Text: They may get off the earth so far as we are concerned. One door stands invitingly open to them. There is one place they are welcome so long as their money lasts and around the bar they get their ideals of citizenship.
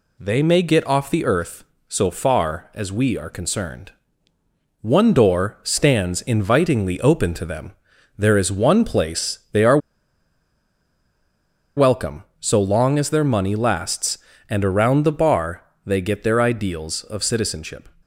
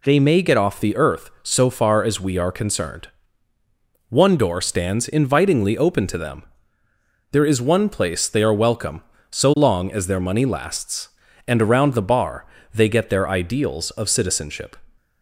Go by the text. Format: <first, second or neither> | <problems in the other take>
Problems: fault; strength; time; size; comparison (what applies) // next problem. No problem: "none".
second | pauses between "are" and "welcome"; strong; at 9.7 s; 1.9 s long // pauses between "bar" and "they"; slight; at 15.6 s; 0.24 s long; slight in the second